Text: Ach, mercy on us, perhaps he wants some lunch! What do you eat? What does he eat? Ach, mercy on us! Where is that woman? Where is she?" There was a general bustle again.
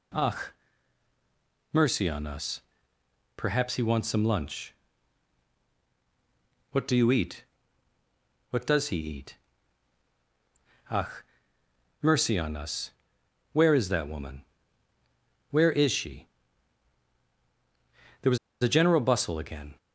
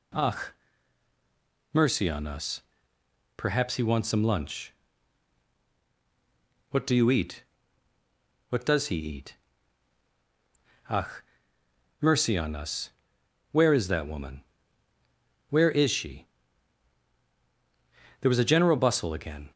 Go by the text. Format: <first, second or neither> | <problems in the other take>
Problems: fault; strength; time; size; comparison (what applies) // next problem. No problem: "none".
second | pauses between "was" and "a"; slight; at 18.3 s; 0.25 s long